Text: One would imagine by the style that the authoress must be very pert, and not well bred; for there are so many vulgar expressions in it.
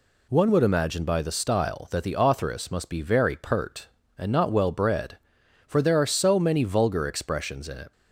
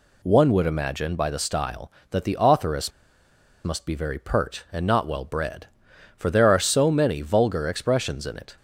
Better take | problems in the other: first | pauses between "authoress" and "must"; noticeable; at 2.9 s; 0.75 s long

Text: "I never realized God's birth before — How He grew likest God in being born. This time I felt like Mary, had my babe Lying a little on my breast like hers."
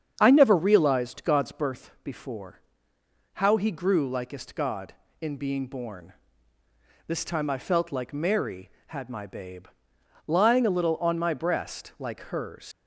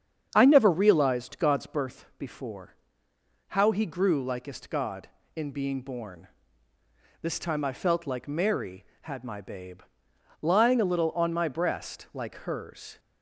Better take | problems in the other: second | starts louder than the rest; strong; until 1.1 s; 7.5 dB; strong in the second // pauses between "babe" and "Lying"; noticeable; at 9.6 s; 0.62 s long; noticeable in the second // leaves "hers" unfinished; at 12.7 s; 130 ms

